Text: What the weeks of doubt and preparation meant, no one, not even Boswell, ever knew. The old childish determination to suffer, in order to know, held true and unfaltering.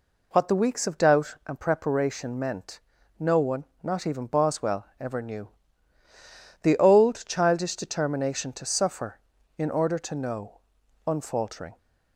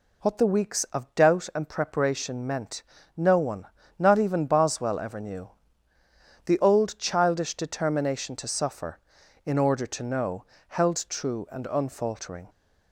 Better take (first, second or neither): second